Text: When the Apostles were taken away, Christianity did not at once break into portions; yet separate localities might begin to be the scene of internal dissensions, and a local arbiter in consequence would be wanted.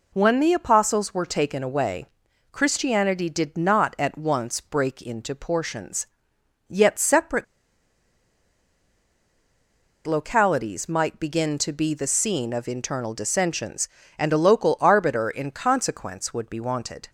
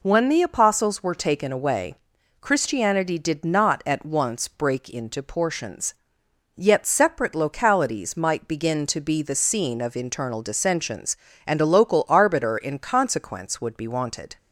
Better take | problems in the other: second | pauses between "separate" and "localities"; strong; at 7.4 s; 2.6 s long

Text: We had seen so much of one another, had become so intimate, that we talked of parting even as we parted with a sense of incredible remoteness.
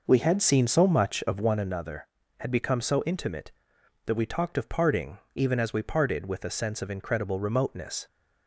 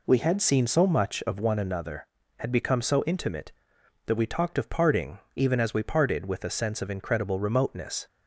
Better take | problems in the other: second | starts louder than the rest; noticeable; until 1.6 s; 5.5 dB // pauses between "parting" and "even"; slight; at 5.1 s; 0.18 s long; slight in the second

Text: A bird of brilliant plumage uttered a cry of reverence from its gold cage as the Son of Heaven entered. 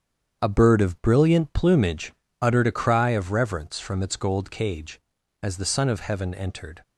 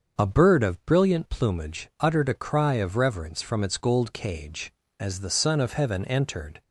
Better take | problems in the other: second | gets quieter; strong; throughout; 7.5 dB // starts louder than the rest; strong; until 1.4 s; 8 dB; also in the second // pauses between "plumage" and "uttered"; slight; at 2.1 s; 0.28 s long

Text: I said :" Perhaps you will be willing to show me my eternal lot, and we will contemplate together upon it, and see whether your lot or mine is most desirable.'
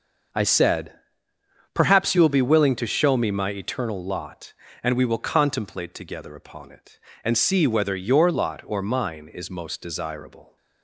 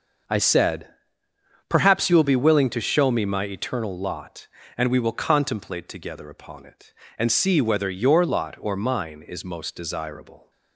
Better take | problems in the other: neither | none

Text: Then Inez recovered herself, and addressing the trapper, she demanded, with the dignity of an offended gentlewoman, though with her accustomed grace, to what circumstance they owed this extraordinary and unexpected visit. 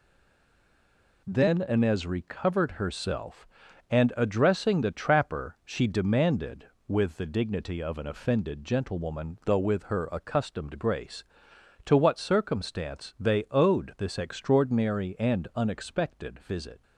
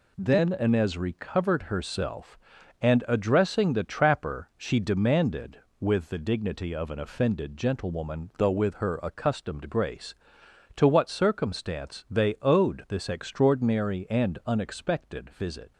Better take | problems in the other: second | stays silent before the first word; noticeable; until 1.2 s; 1.2 s long

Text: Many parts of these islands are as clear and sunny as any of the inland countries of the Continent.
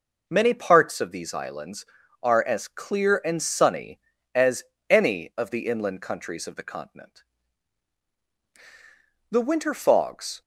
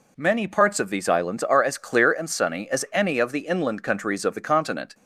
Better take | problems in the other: second | pauses between "as" and "any"; slight; at 4.6 s; 0.26 s long // goes on to say "The winter fogs"; noticeable; from 9.3 s on; 1.1 s long

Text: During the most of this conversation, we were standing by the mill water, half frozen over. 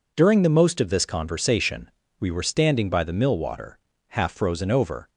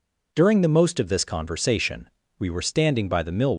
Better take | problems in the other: first | stops before "water half frozen over"; at 3.5 s

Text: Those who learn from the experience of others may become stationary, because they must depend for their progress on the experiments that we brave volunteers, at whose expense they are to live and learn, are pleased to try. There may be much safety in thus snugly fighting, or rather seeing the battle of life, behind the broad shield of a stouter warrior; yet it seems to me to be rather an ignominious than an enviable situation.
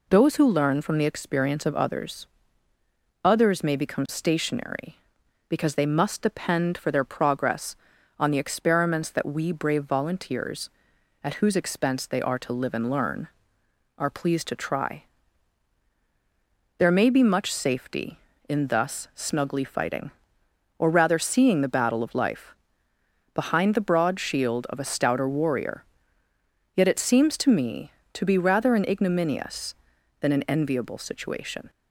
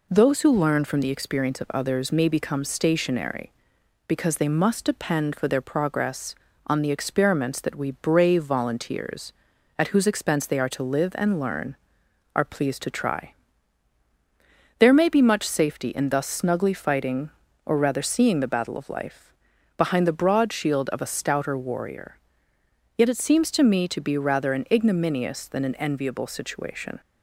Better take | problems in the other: second | says "others" twice; at 3.2 s

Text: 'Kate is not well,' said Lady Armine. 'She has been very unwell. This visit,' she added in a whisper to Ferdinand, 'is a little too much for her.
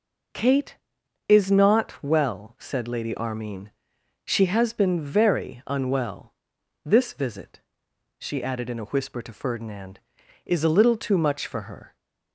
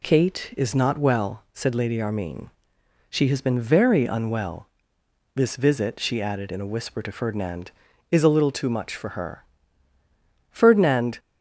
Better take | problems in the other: first | goes on to say "Ferdinand"; noticeable; from 10.5 s on; 0.68 s long

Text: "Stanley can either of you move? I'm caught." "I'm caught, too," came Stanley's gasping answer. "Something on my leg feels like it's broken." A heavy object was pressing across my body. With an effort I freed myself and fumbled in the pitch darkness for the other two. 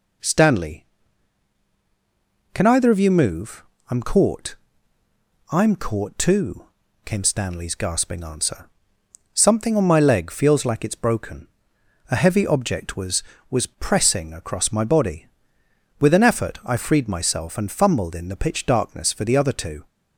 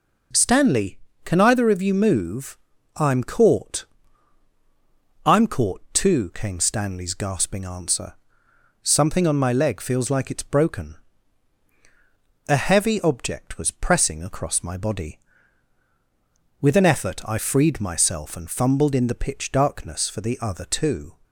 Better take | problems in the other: second | says "was" twice; at 13.4 s

